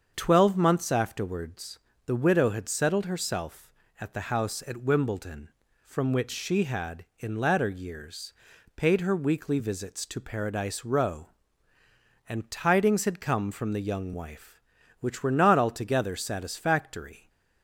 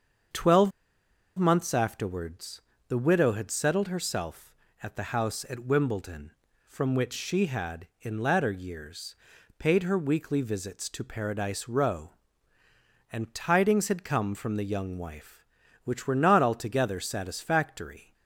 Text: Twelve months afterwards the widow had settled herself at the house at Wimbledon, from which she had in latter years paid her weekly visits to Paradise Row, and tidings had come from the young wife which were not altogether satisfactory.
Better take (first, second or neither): first